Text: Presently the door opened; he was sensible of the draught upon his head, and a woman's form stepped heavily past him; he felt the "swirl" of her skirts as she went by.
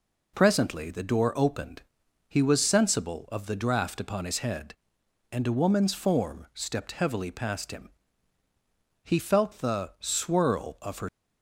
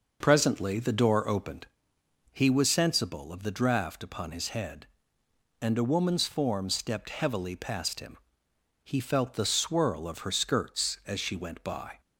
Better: second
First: stops before "skirts as she went by"; at 11.0 s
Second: none

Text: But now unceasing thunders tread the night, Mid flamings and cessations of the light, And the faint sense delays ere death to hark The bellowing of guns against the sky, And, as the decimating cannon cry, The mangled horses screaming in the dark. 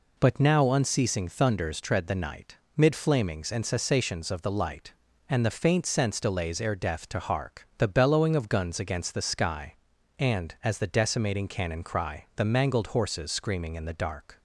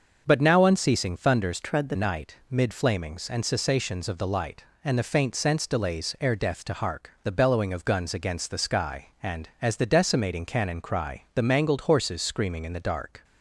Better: first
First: none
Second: starts louder than the rest; until 1.2 s; 6.5 dB // changes voice from "tread" to "the"; from 1.6 to 1.9 s; 0.3 s long

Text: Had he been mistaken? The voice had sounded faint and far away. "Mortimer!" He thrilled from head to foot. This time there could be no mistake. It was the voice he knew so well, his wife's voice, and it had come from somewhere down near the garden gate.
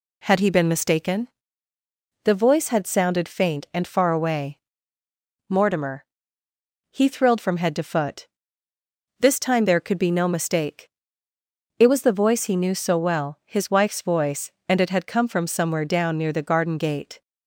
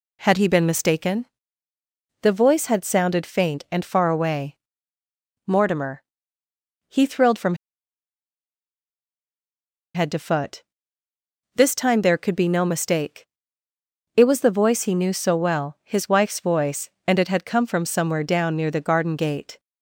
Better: first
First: none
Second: pauses between "from" and "head"; strong; at 7.5 s; 2.4 s long

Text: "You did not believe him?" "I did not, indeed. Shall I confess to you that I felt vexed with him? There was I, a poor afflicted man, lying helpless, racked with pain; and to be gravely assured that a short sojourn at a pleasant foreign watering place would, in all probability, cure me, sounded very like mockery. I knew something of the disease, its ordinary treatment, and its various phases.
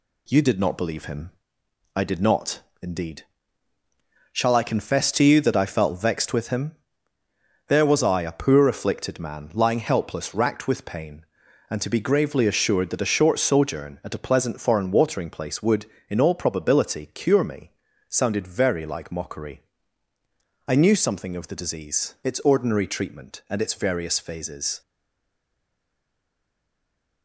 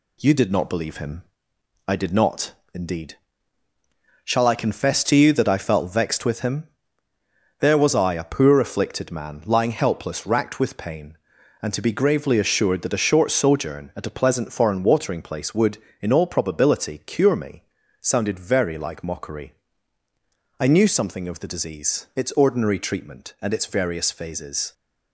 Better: second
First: stays silent after the last word; from 24.8 s on; 2.4 s long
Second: none

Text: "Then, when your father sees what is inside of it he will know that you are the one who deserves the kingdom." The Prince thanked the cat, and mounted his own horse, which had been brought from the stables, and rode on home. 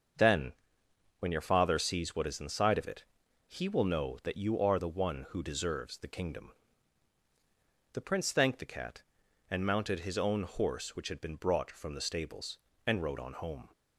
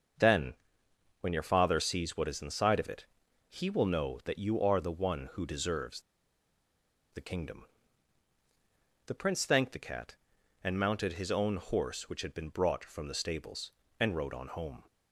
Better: first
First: starts louder than the rest; until 1.8 s; 6.5 dB // pauses between "it" and "he"; at 3.0 s; 0.42 s long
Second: starts louder than the rest; until 1.8 s; 6.5 dB // pauses between "it" and "he"; at 3.0 s; 0.42 s long // pauses between "deserves" and "the"; at 6.0 s; 1.1 s long

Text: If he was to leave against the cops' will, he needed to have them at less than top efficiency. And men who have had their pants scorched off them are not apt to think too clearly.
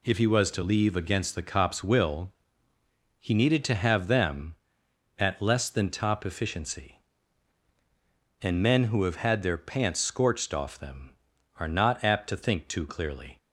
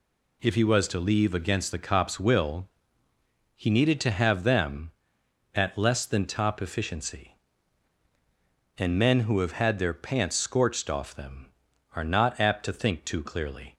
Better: neither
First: none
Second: none

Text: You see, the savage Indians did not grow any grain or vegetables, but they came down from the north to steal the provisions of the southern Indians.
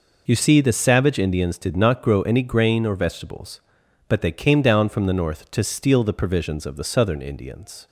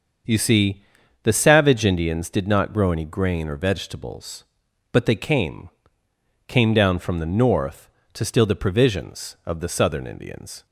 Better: first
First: none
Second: starts louder than the rest; until 1.7 s; 7 dB // says "came" twice; at 6.4 s

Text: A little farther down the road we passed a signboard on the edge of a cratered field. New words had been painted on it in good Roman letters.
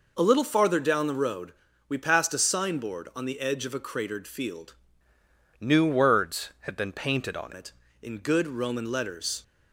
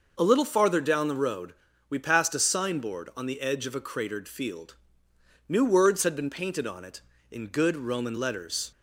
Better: second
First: pauses between "road" and "we"; slight; at 1.5 s; 0.34 s long // changes voice from "New" to "on"; from 5.5 to 7.5 s; 2.0 s long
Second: pauses between "road" and "we"; slight; at 1.5 s; 0.34 s long

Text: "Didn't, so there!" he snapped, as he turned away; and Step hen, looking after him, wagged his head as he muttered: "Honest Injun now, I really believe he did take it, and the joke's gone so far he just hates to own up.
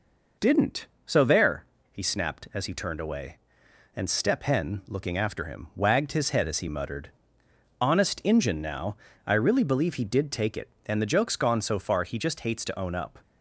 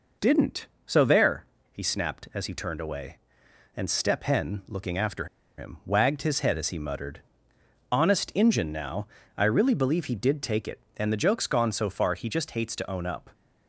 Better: first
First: none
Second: pauses between "after" and "him"; slight; at 5.2 s; 0.32 s long

